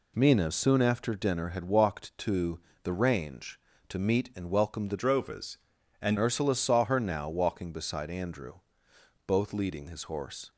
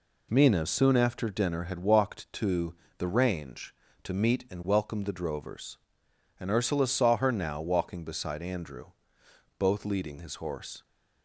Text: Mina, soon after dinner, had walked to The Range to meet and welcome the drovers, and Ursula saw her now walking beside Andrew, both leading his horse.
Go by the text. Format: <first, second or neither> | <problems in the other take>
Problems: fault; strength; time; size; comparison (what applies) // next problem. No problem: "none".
second | pauses between "to" and "The"; slight; at 2.6 s; 0.24 s long; slight in the second // changes voice from "drovers" to "and"; from 4.9 to 6.1 s; 1.2 s long